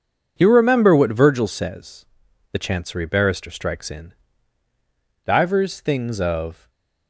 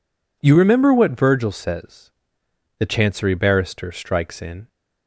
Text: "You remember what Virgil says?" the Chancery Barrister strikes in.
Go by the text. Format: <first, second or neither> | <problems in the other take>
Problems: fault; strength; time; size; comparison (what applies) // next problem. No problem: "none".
second | goes on to say "Divers things of"; from 5.2 s on; 1.4 s long // stays silent after the last word; slight; from 6.5 s on; 0.5 s long